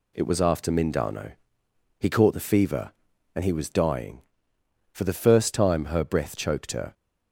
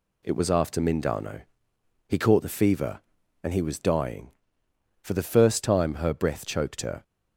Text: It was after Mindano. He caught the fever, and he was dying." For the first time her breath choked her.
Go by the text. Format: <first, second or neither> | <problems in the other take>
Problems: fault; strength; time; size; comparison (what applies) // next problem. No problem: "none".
neither | none